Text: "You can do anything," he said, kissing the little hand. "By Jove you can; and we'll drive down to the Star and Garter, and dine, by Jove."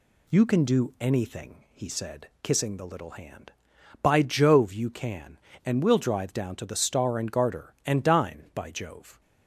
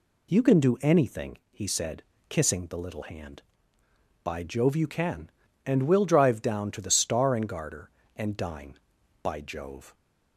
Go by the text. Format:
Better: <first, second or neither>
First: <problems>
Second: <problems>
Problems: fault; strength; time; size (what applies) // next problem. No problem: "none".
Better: neither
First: none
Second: none